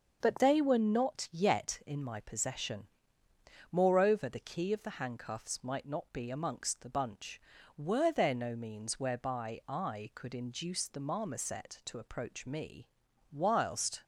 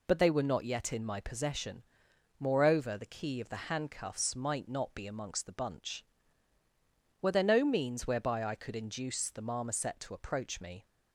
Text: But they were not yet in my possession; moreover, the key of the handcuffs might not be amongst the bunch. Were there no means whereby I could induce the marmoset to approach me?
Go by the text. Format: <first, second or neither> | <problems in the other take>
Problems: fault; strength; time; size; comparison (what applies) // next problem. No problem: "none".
second | starts louder than the rest; until 1.2 s; 6.5 dB // goes on to say "Whilst"; noticeable; from 13.3 s on; 0.72 s long